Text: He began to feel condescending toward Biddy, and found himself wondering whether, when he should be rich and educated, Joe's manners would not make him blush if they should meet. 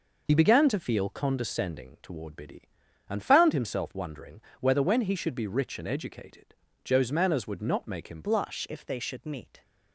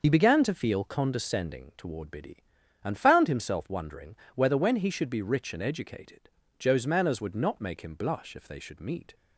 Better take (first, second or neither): second